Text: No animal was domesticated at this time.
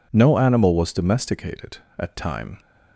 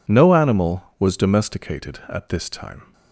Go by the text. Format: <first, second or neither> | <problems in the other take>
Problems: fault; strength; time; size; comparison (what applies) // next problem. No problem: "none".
second | skips "this"; at 2.1 s